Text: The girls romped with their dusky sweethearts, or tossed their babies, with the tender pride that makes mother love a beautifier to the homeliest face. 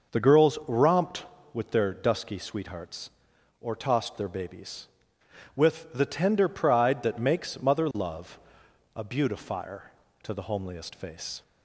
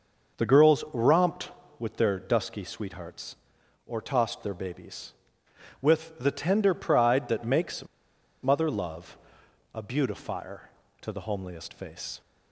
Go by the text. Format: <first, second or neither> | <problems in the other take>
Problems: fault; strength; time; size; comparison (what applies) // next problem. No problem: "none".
first | starts louder than the rest; noticeable; until 1.4 s; 6 dB; noticeable in the first // pauses between "makes" and "mother"; noticeable; at 7.8 s; 0.56 s long // pauses between "love" and "a"; noticeable; at 9.1 s; 0.56 s long; noticeable in the first